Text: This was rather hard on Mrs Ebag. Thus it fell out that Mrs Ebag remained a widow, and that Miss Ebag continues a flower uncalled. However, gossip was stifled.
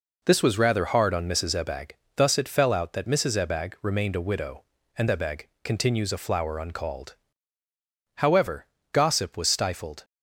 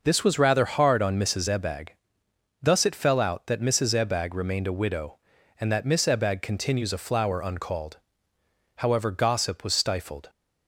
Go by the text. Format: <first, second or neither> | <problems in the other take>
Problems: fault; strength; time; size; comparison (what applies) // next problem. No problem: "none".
second | skips "that Miss"; at 5.0 s // pauses between "Ebag" and "continues"; slight; at 5.4 s; 0.16 s long